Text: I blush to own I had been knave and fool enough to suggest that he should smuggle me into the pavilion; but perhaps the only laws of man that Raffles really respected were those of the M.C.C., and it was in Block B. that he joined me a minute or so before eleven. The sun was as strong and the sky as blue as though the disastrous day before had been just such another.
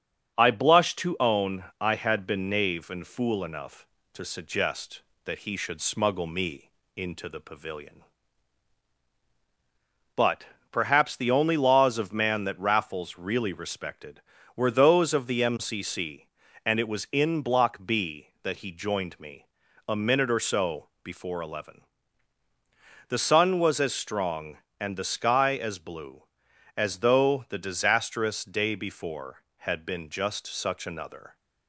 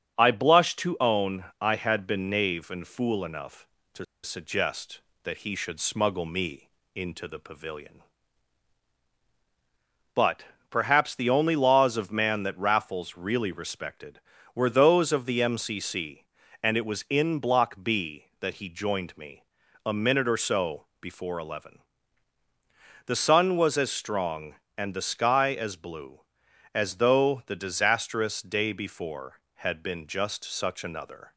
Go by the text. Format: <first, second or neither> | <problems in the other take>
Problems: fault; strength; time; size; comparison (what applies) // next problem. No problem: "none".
first | starts louder than the rest; until 1.2 s; 7 dB; also in the first // pauses between "own" and "I"; slight; at 1.4 s; 0.16 s long; slight in the first // pauses between "to" and "suggest"; slight; at 4.0 s; 0.19 s long // pauses between "me" and "into"; slight; at 6.7 s; 0.24 s long; slight in the first // pauses between "but" and "perhaps"; slight; at 10.4 s; 0.26 s long; slight in the first // pauses between "me" and "a"; at 19.4 s; 0.42 s long; also in the first